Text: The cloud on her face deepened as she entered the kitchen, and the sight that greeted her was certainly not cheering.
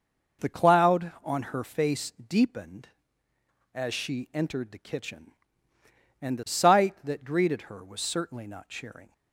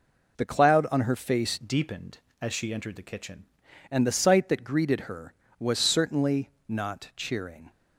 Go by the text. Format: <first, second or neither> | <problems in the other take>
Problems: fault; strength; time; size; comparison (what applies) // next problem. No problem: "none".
first | changes voice from "deepened" to "kitchen"; from 1.6 to 3.4 s; 1.8 s long // pauses between "certainly" and "not"; slight; at 6.5 s; 0.18 s long